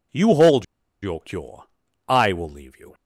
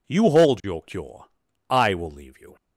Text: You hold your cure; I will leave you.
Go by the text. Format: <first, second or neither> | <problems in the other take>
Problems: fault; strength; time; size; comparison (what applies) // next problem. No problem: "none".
second | pauses between "hold" and "your"; at 0.6 s; 0.37 s long